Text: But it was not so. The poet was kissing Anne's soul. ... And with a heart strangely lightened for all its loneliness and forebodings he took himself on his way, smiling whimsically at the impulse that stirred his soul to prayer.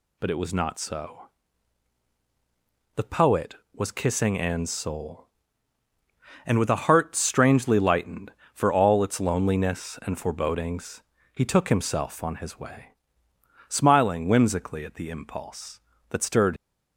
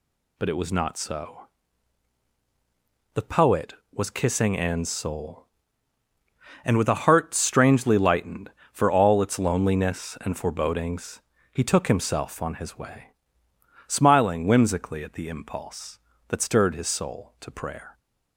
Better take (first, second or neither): second